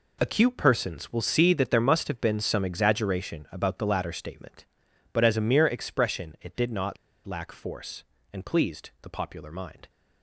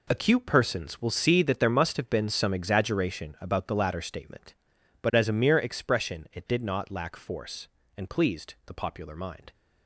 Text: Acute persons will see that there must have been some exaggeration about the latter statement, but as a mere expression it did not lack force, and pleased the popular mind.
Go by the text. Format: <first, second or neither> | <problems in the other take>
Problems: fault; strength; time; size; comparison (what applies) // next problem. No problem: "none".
second | pauses between "not" and "lack"; slight; at 6.9 s; 0.29 s long